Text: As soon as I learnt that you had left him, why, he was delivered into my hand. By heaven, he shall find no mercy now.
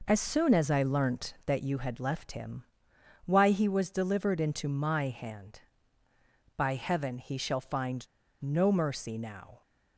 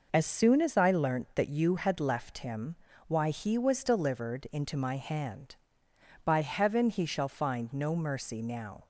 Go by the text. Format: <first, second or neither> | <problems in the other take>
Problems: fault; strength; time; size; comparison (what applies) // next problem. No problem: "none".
second | pauses between "find" and "no"; slight; at 8.0 s; 0.36 s long